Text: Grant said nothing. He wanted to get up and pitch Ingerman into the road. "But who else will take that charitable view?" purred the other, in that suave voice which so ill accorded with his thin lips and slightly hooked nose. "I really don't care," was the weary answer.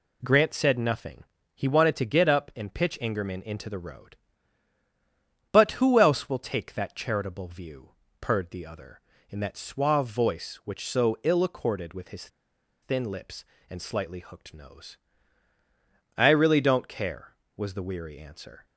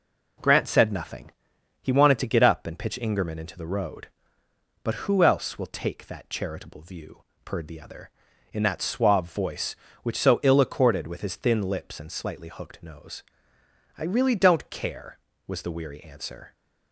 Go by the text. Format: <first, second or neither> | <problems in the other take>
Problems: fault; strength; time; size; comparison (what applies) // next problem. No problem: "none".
second | pauses between "his" and "thin"; noticeable; at 12.2 s; 0.55 s long